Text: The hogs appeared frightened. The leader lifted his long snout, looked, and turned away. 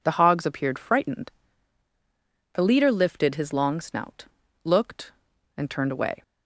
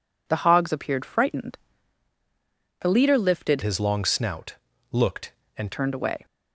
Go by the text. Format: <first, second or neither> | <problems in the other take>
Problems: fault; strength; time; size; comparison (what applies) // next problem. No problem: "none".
first | changes voice from "his" to "and"; from 3.6 to 5.7 s; 2.1 s long